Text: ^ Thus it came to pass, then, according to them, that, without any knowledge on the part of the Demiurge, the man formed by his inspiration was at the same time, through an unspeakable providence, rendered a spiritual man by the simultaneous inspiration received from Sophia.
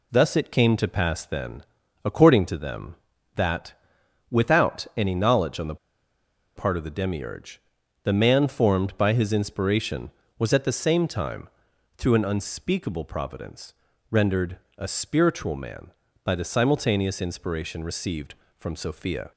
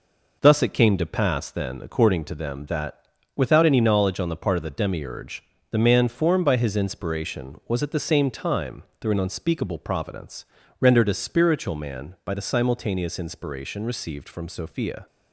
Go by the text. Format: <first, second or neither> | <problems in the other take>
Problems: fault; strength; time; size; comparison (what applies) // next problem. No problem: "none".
second | pauses between "the" and "part"; noticeable; at 5.7 s; 0.80 s long // pauses between "rendered" and "a"; slight; at 14.5 s; 0.20 s long